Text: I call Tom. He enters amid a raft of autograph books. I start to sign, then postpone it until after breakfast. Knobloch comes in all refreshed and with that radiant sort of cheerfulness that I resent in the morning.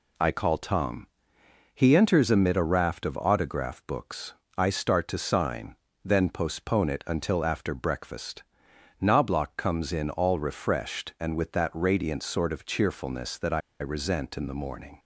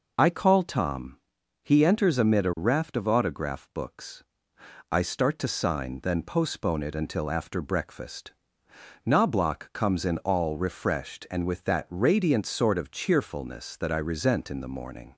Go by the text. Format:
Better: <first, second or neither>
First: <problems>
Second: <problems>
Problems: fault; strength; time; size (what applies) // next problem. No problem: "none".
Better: second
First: pauses between "I" and "resent"; slight; at 13.5 s; 0.20 s long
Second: none